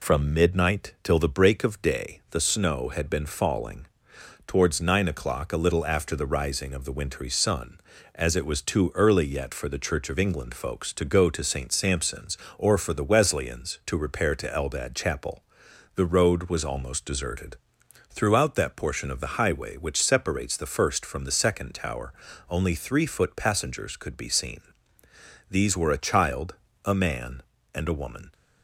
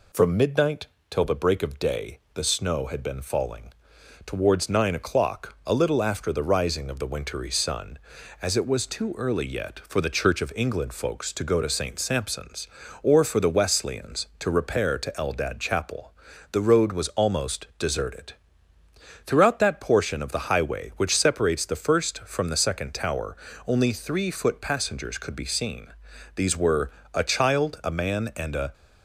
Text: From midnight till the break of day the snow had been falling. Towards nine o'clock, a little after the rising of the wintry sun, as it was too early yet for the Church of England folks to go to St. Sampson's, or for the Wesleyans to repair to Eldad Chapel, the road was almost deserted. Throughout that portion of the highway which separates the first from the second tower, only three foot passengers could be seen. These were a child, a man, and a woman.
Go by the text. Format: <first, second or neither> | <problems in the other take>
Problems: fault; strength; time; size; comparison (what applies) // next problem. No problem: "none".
first | pauses between "midnight" and "till"; slight; at 0.8 s; 0.24 s long // pauses between "day" and "the"; slight; at 2.1 s; 0.16 s long // pauses between "were" and "a"; slight; at 26.9 s; 0.24 s long // stops before "woman"; at 28.7 s